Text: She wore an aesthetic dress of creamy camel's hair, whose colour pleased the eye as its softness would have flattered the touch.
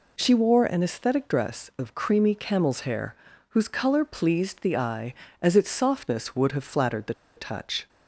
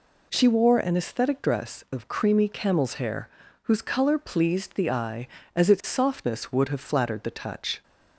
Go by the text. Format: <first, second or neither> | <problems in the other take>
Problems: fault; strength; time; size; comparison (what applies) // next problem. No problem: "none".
second | pauses between "the" and "touch"; slight; at 7.1 s; 0.22 s long